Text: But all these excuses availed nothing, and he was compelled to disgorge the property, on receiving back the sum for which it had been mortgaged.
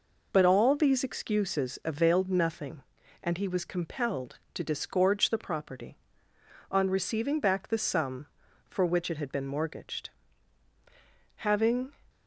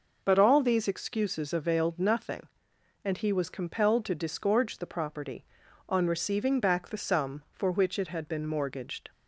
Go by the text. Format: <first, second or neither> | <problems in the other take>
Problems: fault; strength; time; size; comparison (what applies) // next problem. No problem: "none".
second | goes on to say "Having"; from 11.3 s on; 0.54 s long